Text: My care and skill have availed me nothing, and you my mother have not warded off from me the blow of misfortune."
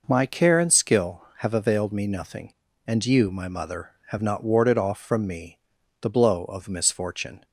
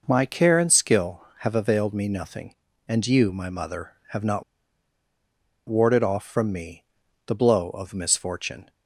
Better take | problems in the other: first | pauses between "not" and "warded"; at 4.4 s; 1.2 s long // pauses between "me" and "the"; at 6.8 s; 0.40 s long; also in the first

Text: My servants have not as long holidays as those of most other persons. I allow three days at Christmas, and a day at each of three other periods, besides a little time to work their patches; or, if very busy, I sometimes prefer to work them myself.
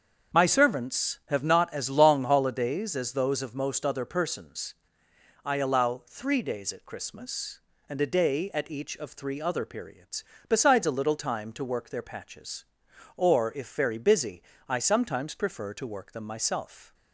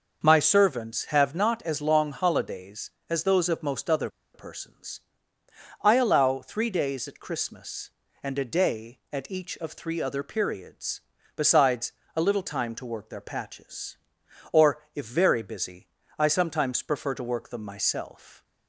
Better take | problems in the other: first | starts louder than the rest; noticeable; until 1.2 s; 6 dB; strong in the first // pauses between "other" and "persons"; slight; at 4.0 s; 0.26 s long // pauses between "besides" and "a"; slight; at 11.9 s; 0.22 s long

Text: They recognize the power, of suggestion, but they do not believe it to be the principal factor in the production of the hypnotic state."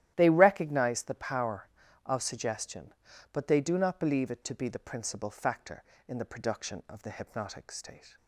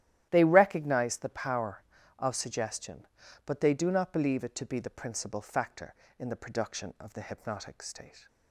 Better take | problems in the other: neither | starts louder than the rest; strong; the same in both

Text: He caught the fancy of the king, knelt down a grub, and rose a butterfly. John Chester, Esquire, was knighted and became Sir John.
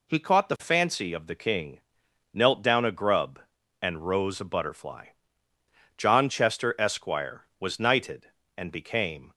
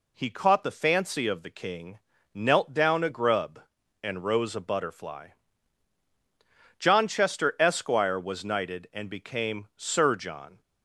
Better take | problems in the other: second | stops before "Sir John"; at 9.3 s

